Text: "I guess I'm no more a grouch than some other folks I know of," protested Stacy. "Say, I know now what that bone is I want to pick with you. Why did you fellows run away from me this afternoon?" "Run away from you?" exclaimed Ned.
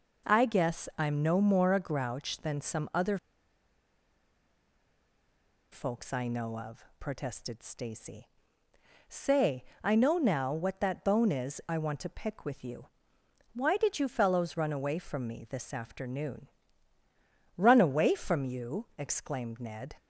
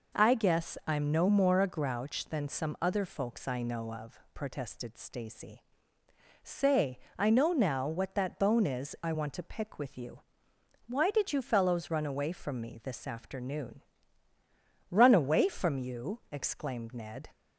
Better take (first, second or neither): second